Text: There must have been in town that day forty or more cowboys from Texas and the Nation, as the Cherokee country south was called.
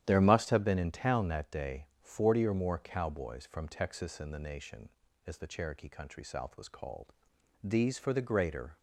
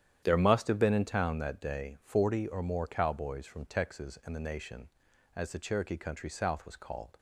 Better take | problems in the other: second | starts louder than the rest; strong; until 1.0 s; 10.5 dB; strong in the second // goes on to say "These for the greater"; noticeable; from 7.6 s on; 1.1 s long

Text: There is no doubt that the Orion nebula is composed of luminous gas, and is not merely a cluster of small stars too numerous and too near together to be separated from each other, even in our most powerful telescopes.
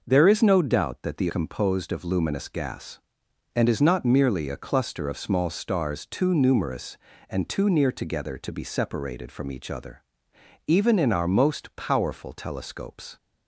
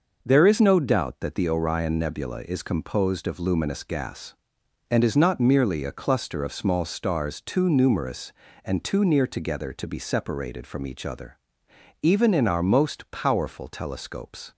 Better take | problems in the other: second | skips "Orion nebula is"; at 1.2 s

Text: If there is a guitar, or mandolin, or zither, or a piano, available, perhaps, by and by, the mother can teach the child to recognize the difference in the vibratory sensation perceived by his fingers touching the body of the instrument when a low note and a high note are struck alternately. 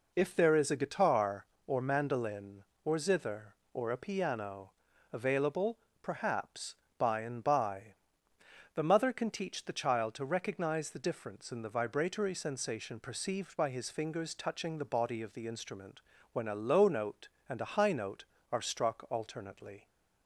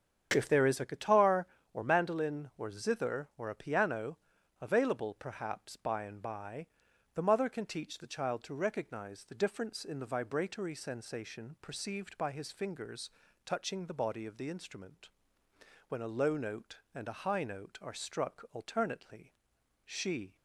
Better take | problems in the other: first | starts louder than the rest; strong; until 1.3 s; 7.5 dB // pauses between "fingers" and "touching"; slight; at 13.0 s; 0.36 s long // pauses between "instrument" and "when"; noticeable; at 15.0 s; 0.80 s long; slight in the first // goes on to say "She"; from 19.8 s on; 0.52 s long

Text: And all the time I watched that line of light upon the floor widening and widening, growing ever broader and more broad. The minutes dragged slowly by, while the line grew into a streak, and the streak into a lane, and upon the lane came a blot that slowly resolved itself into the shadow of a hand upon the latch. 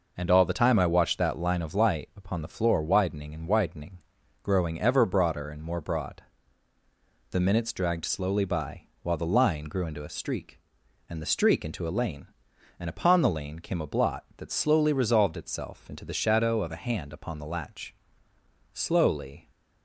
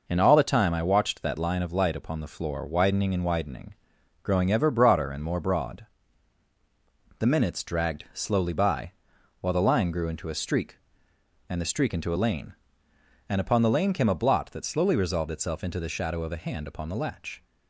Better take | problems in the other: second | goes on to say "Slowly"; noticeable; from 18.7 s on; 0.76 s long

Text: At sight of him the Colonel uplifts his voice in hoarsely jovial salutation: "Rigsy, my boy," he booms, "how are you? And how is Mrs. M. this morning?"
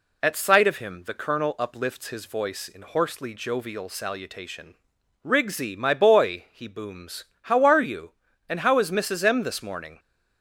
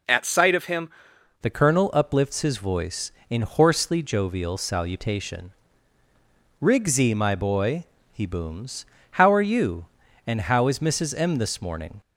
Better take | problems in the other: first | changes voice at "the"; from 1.4 s on; 10.6 s long

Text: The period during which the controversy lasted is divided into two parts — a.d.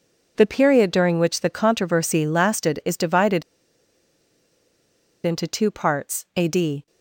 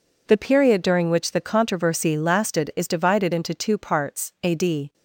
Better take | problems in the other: second | pauses between "divided" and "into"; strong; at 3.4 s; 1.8 s long

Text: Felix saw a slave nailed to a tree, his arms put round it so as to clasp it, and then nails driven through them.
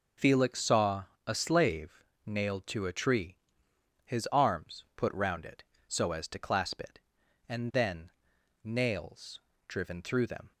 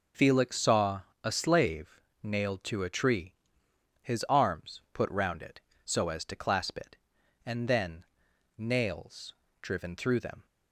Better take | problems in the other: neither | pauses between "saw" and "a"; slight; the same in both // pauses between "slave" and "nailed"; slight; the same in both // pauses between "then" and "nails"; noticeable; the same in both // pauses between "nails" and "driven"; slight; the same in both

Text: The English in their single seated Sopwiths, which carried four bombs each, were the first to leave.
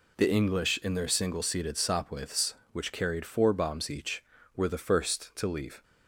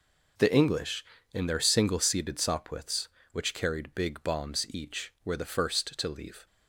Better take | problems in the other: first | says "big" for "four"; at 3.9 s

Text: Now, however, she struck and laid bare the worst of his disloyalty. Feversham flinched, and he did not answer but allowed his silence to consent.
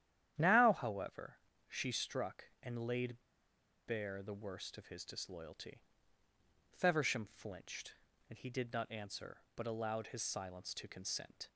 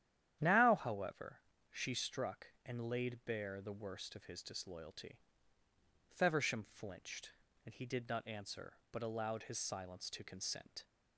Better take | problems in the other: second | starts louder than the rest; strong; until 1.7 s; 10.5 dB; strong in the second // pauses between "laid" and "bare"; noticeable; at 3.1 s; 0.71 s long

